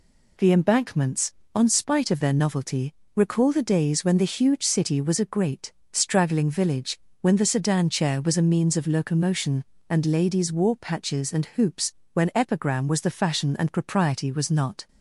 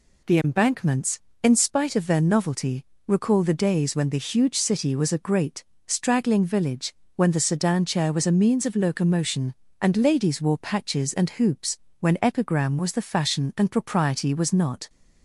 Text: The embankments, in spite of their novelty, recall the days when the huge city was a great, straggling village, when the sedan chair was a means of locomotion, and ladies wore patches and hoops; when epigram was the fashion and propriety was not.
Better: second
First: says "on" for "in"; at 1.5 s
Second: none

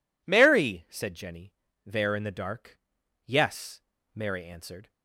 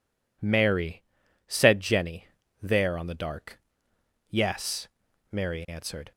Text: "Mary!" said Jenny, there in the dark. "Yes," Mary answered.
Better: first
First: none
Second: says "on" for "in"; at 2.9 s

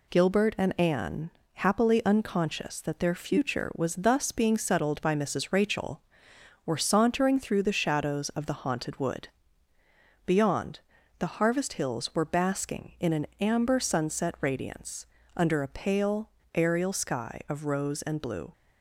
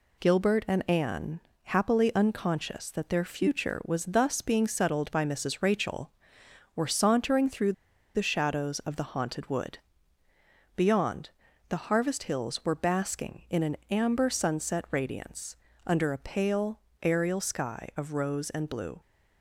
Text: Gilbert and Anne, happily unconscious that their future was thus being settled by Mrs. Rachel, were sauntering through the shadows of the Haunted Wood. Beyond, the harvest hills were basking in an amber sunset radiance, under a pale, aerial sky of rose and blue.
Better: first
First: none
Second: pauses between "through" and "the"; at 7.7 s; 0.43 s long

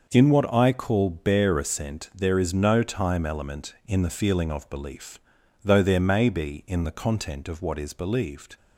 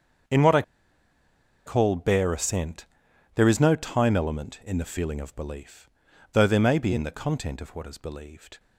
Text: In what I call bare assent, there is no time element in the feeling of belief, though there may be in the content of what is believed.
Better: first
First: starts louder than the rest; until 1.1 s; 6 dB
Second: starts louder than the rest; strong; until 2.3 s; 7 dB // pauses between "I" and "call"; at 0.6 s; 1.0 s long

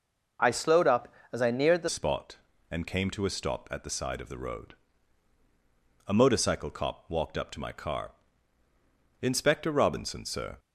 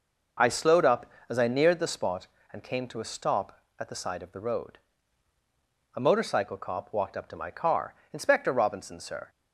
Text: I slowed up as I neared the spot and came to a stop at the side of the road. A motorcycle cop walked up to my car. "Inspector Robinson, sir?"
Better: second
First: changes voice at "spot"; from 1.8 s on; 8.7 s long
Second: none

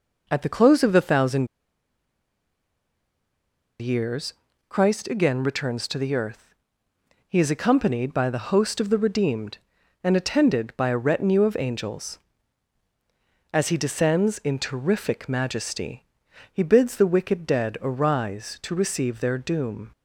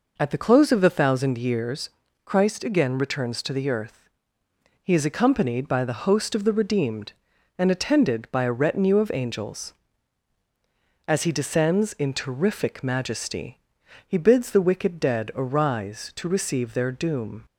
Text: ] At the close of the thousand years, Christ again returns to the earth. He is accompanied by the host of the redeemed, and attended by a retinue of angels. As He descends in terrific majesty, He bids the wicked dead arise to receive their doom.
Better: second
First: pauses between "thousand" and "years"; strong; at 1.4 s; 2.3 s long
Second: none

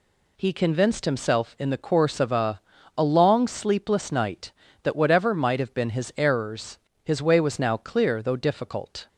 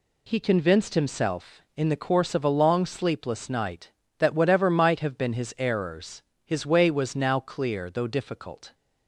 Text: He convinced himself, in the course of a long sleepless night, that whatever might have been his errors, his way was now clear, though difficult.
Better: second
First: says "a" twice; at 2.9 s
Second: none

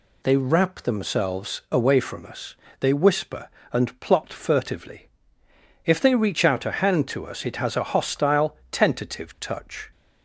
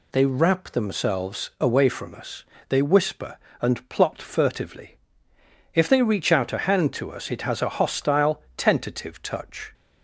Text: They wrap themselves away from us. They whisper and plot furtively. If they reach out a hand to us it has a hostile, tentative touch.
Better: neither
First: none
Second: none

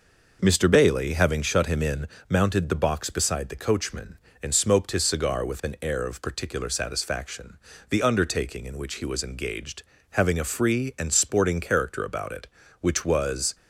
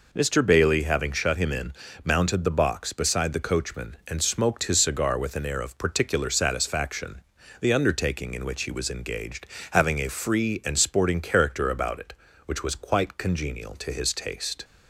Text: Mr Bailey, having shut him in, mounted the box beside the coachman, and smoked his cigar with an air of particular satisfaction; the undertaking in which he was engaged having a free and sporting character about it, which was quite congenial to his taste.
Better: second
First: pauses between "engaged" and "having"; slight; at 9.8 s; 0.28 s long // stops before "quite congenial to his taste"; at 13.5 s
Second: pauses between "engaged" and "having"; slight; at 9.4 s; 0.24 s long

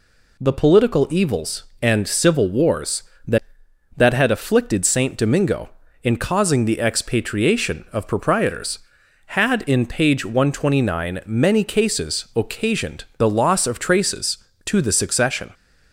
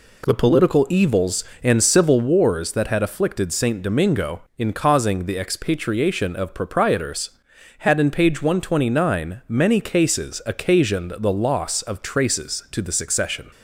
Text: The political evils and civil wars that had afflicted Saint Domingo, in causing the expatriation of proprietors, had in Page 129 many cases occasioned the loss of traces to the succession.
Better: second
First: says "that" twice; at 3.9 s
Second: none

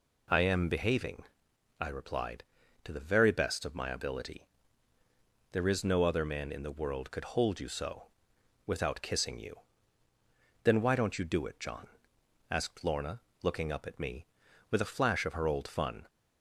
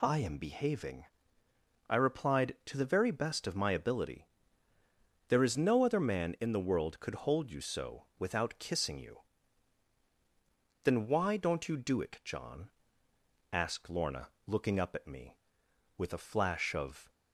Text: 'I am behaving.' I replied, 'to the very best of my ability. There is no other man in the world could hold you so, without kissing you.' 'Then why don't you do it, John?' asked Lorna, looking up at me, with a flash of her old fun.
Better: first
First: none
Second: stops before "her old fun"; at 17.1 s

